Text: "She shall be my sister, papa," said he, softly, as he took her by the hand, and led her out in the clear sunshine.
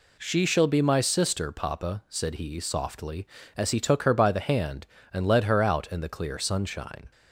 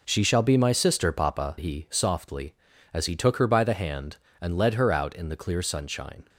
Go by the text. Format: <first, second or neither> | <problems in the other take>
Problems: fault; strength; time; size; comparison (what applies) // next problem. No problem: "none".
first | skips "said"; at 1.5 s